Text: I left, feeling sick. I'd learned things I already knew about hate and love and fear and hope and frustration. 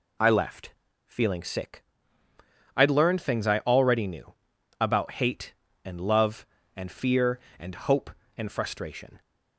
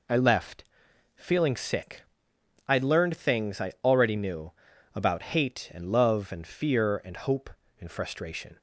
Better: neither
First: pauses between "knew" and "about"; noticeable; at 4.3 s; 0.48 s long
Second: pauses between "knew" and "about"; at 4.5 s; 0.44 s long

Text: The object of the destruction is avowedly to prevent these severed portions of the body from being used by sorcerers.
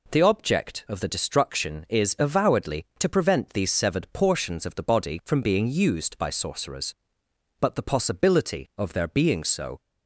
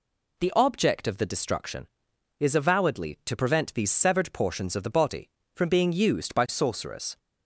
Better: second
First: goes on to say "But the possibility of their being so"; strong; from 7.5 s on; 2.2 s long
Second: none

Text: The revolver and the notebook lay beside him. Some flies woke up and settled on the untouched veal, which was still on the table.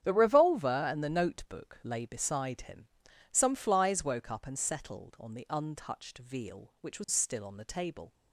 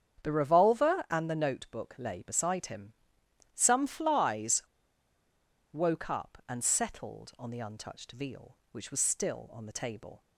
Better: first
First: starts louder than the rest; strong; until 1.0 s; 9.5 dB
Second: starts louder than the rest; strong; until 1.2 s; 8 dB // pauses between "flies" and "woke"; at 4.6 s; 1.1 s long

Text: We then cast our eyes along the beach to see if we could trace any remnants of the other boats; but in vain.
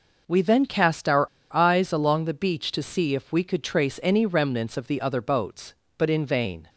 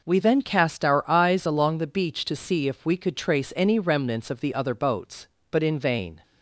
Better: second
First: pauses between "our" and "eyes"; slight; at 1.2 s; 0.24 s long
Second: none

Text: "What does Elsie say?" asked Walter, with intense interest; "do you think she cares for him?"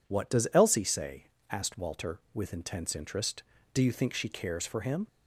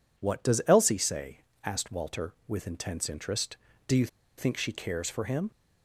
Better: first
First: none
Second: pauses between "you" and "think"; slight; at 4.0 s; 0.30 s long

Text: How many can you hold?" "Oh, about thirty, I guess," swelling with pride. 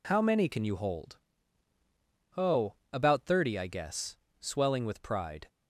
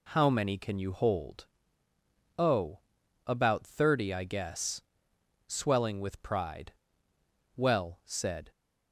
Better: first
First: none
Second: goes on to say "Well said"; noticeable; from 7.5 s on; 0.94 s long

